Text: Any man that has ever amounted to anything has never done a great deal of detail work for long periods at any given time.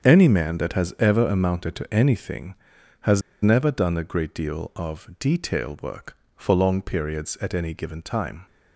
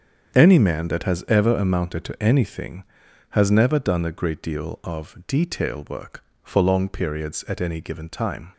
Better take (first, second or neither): second